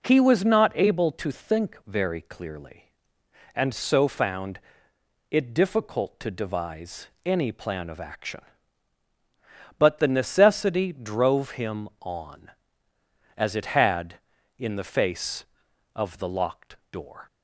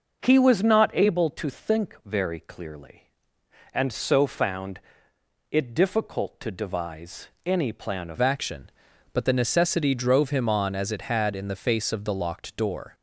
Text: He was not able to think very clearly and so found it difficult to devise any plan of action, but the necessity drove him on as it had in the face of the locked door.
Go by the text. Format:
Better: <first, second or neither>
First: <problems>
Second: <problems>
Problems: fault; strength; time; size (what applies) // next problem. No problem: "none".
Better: first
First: pauses between "found" and "it"; noticeable; at 4.5 s; 0.72 s long // pauses between "devise" and "any"; slight; at 7.0 s; 0.18 s long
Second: pauses between "found" and "it"; noticeable; at 4.7 s; 0.72 s long // pauses between "devise" and "any"; slight; at 7.2 s; 0.18 s long // changes voice at "action"; from 8.1 s on; 4.8 s long